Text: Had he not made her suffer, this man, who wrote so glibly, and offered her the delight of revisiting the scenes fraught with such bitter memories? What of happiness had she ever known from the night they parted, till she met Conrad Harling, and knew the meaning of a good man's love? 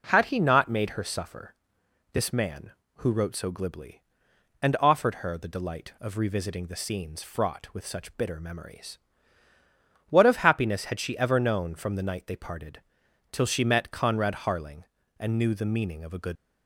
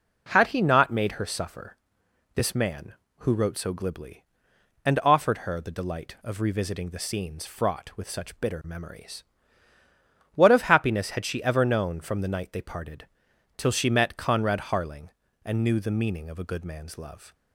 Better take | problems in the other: second | stops before "man's love"; at 16.3 s

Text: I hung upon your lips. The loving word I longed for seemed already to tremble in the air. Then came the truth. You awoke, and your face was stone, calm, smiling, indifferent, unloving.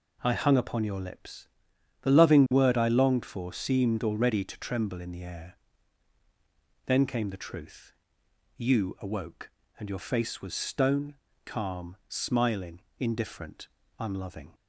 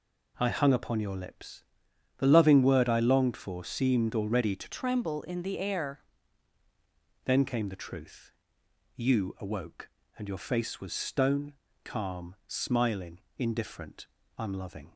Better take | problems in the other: first | changes voice from "tremble" to "air"; from 4.6 to 6.0 s; 1.4 s long

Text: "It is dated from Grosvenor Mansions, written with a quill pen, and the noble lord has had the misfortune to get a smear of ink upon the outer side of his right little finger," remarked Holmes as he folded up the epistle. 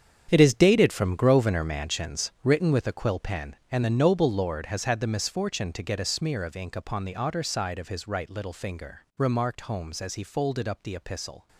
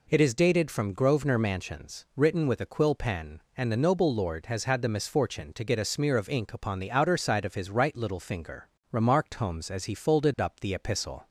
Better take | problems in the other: second | gets quieter; strong; throughout; 13 dB

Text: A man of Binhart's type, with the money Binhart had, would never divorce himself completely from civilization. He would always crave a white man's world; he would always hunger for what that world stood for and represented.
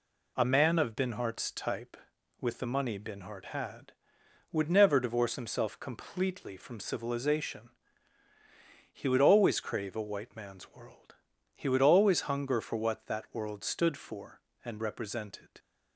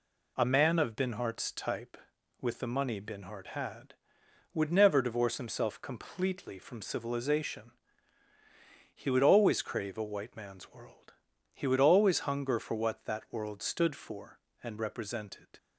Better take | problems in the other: neither | none

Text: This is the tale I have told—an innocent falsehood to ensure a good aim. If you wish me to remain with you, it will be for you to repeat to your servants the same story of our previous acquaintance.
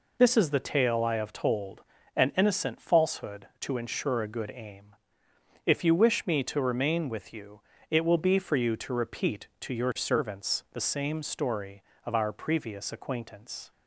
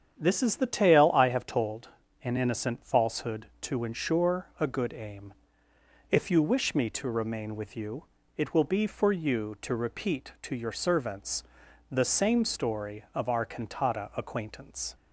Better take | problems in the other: first | starts louder than the rest; strong; until 1.1 s; 8 dB // pauses between "servants" and "the"; noticeable; at 11.4 s; 0.48 s long // says "cantata" for "previous"; at 13.4 s

